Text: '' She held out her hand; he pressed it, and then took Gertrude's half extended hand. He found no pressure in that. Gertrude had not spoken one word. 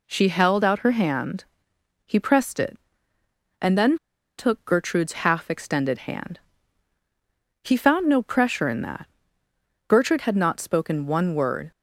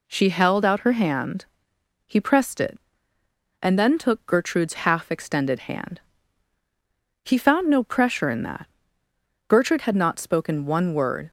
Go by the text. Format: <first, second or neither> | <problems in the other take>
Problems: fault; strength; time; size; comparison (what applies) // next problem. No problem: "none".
second | pauses between "then" and "took"; at 3.9 s; 0.41 s long